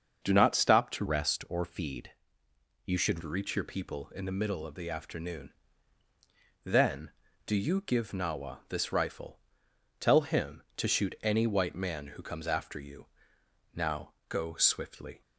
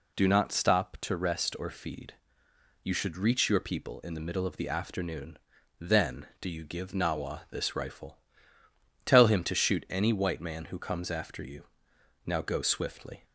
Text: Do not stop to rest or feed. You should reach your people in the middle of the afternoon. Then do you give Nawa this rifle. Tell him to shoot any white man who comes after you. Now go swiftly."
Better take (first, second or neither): second